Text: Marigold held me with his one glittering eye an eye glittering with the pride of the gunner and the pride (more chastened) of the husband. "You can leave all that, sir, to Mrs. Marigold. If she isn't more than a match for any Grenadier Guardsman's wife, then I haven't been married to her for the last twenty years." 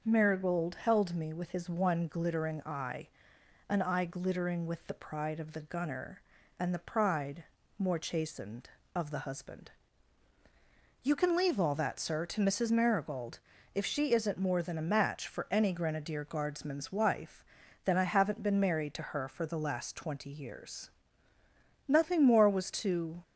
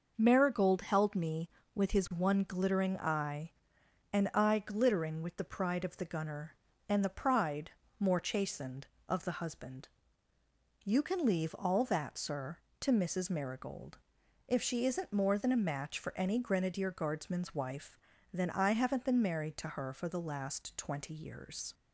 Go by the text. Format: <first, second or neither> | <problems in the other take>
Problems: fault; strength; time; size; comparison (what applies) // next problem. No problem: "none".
second | starts louder than the rest; until 1.0 s; 6 dB // pauses between "eye" and "an"; noticeable; at 3.0 s; 0.60 s long; noticeable in the second // goes on to say "Nothing more was to"; noticeable; from 22.0 s on; 1.2 s long